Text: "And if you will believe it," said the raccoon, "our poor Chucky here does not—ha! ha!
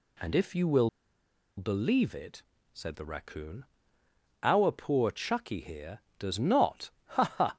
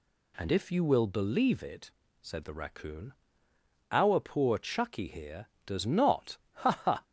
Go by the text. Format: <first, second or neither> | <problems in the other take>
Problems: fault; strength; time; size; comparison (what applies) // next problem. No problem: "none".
second | pauses between "will" and "believe"; noticeable; at 0.8 s; 0.68 s long